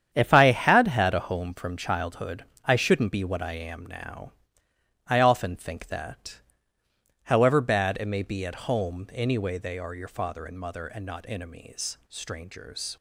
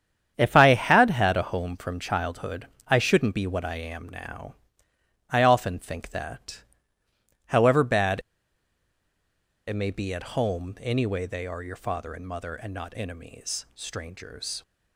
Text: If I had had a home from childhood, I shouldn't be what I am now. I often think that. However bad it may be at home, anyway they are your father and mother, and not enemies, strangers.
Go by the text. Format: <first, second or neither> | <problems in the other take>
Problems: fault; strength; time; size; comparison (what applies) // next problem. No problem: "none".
first | starts louder than the rest; strong; until 1.4 s; 8.5 dB; strong in the first // pauses between "bad" and "it"; strong; at 8.1 s; 1.4 s long